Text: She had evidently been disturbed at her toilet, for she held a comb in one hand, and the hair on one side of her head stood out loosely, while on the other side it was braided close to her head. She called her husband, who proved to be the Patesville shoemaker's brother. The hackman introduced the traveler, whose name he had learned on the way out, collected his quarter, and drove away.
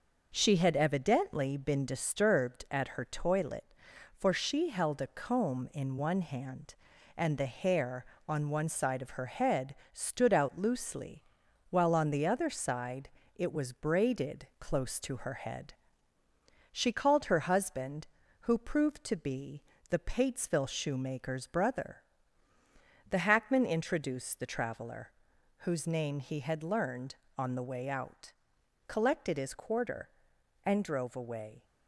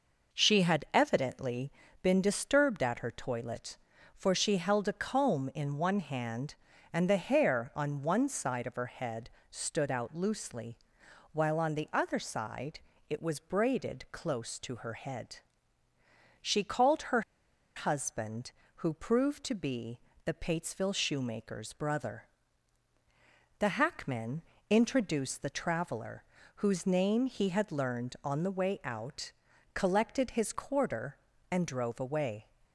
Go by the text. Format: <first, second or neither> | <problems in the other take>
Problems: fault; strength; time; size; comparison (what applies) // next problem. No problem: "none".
first | pauses between "evidently" and "been"; slight; at 1.7 s; 0.32 s long // pauses between "head" and "stood"; slight; at 9.2 s; 0.22 s long; slight in the first // pauses between "side" and "it"; slight; at 12.7 s; 0.30 s long; slight in the first // pauses between "her" and "husband"; noticeable; at 17.2 s; 0.55 s long // pauses between "be" and "the"; slight; at 19.9 s; 0.26 s long; slight in the first // pauses between "hackman" and "introduced"; slight; at 24.4 s; 0.26 s long